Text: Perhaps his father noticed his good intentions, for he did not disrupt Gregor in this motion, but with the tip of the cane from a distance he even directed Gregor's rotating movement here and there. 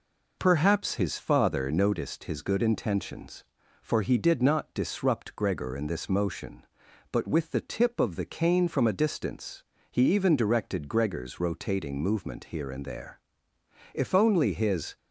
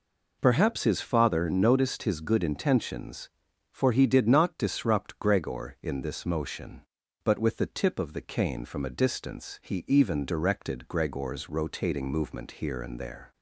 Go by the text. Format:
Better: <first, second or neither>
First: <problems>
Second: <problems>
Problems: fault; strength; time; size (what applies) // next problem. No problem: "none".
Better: second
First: pauses between "distance" and "he"; slight; at 9.6 s; 0.26 s long // goes on to say "If only his"; noticeable; from 13.9 s on; 1.0 s long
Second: none